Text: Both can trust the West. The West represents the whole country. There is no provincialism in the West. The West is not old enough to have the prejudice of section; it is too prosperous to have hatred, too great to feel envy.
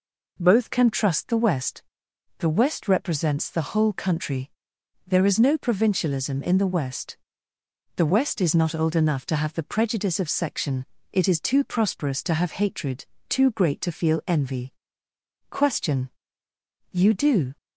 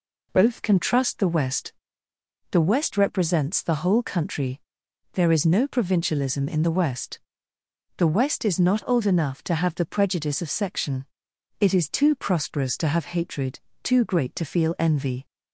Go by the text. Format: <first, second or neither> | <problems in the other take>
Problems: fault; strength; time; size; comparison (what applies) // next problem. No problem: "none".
second | goes on to say "Question You do"; strong; from 15.4 s on; 2.0 s long